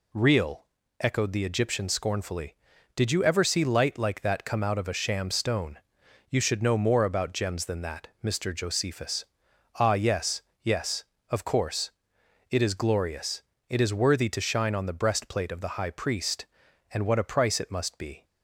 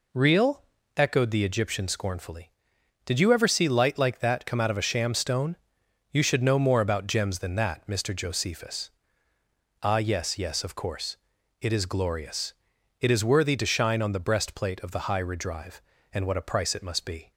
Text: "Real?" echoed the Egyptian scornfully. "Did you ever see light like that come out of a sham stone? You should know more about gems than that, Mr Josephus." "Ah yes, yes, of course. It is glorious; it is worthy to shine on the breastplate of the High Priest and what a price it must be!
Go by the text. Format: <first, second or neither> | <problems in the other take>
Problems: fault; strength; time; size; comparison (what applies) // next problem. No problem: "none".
first | says "Redrive" for "Priest"; at 15.2 s